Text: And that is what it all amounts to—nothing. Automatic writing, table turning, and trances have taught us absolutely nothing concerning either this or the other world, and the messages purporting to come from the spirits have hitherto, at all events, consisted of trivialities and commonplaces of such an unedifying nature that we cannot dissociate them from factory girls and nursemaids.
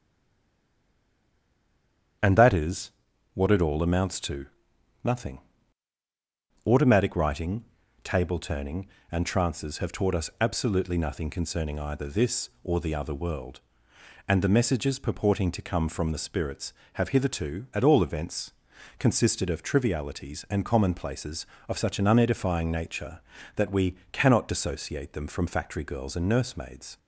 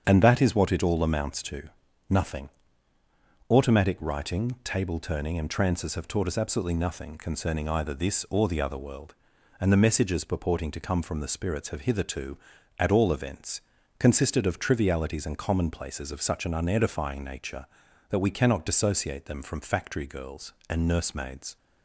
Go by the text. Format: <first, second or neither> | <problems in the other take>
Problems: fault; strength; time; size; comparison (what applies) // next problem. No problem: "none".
second | stays silent before the first word; until 2.2 s; 2.2 s long // starts louder than the rest; strong; until 3.6 s; 8.5 dB; strong in the second // pauses between "is" and "what"; at 2.9 s; 0.42 s long // pauses between "we" and "cannot"; slight; at 23.9 s; 0.16 s long